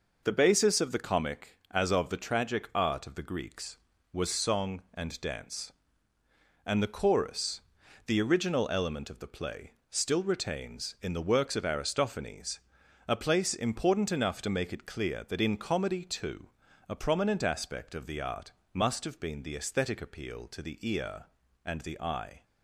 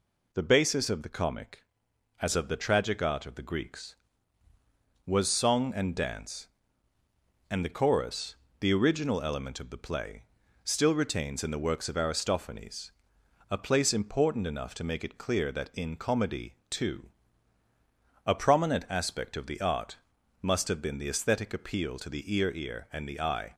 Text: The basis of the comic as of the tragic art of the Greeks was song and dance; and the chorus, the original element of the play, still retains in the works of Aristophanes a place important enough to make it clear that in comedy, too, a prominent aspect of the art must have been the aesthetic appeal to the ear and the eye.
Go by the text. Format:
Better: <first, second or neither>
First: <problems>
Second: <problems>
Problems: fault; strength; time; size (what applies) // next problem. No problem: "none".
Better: first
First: pauses between "Aristophanes" and "a"; noticeable; at 12.6 s; 0.48 s long // pauses between "art" and "must"; slight; at 18.5 s; 0.20 s long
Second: pauses between "Aristophanes" and "a"; noticeable; at 12.9 s; 0.58 s long // pauses between "art" and "must"; noticeable; at 19.9 s; 0.46 s long // says "ear" twice; at 22.5 s